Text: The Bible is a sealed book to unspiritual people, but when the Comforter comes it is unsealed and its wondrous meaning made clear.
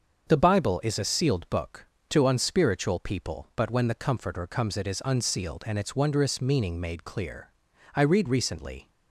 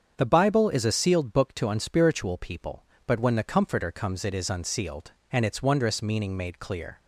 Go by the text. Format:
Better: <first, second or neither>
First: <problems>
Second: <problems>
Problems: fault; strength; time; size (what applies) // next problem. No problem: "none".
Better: second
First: starts louder than the rest; until 1.3 s; 7 dB // goes on to say "I read recently"; noticeable; from 7.9 s on; 0.94 s long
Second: starts louder than the rest; strong; until 1.1 s; 7.5 dB